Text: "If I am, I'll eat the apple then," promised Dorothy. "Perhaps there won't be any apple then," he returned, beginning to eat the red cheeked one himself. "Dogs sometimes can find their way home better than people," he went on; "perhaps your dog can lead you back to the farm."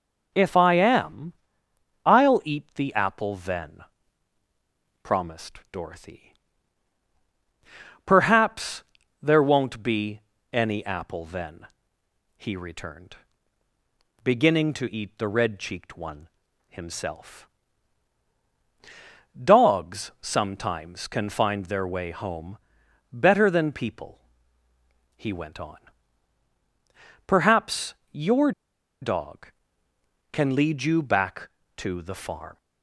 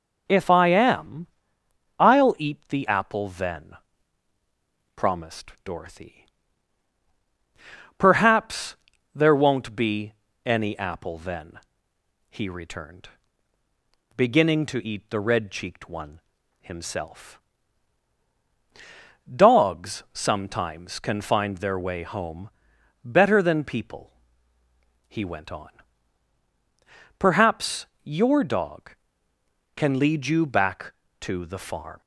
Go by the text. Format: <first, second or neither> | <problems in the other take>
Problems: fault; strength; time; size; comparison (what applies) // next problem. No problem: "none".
second | pauses between "Perhaps" and "there"; at 8.8 s; 0.38 s long; also in the second // pauses between "be" and "any"; slight; at 10.2 s; 0.32 s long; slight in the second // pauses between "one" and "himself"; at 16.2 s; 0.40 s long; also in the second // pauses between "home" and "better"; noticeable; at 22.5 s; 0.54 s long; noticeable in the second // pauses between "perhaps" and "your"; slight; at 27.9 s; 0.16 s long; slight in the second // pauses between "your" and "dog"; noticeable; at 28.5 s; 0.51 s long